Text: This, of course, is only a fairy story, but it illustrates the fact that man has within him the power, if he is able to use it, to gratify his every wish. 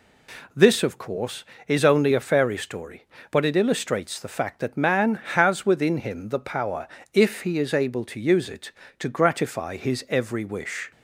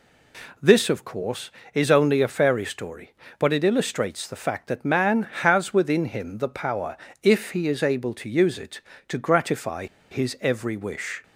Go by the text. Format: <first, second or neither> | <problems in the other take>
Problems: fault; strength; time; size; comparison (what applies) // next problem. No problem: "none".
first | pauses between "gratify" and "his"; slight; at 9.8 s; 0.25 s long